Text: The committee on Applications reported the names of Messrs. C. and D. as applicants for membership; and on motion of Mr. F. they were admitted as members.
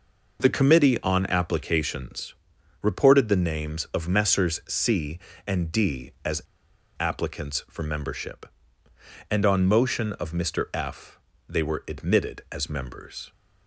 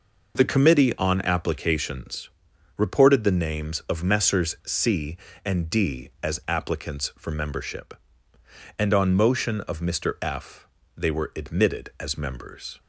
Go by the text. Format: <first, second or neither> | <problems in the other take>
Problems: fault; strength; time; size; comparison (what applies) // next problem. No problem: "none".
second | pauses between "Applications" and "reported"; noticeable; at 2.3 s; 0.48 s long; noticeable in the second // pauses between "as" and "applicants"; noticeable; at 6.4 s; 0.58 s long // pauses between "F" and "they"; slight; at 11.1 s; 0.32 s long; slight in the second